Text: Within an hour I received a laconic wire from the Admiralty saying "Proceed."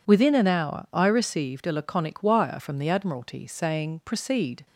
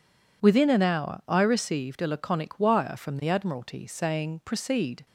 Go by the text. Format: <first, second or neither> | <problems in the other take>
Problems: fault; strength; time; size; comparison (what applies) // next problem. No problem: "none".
neither | none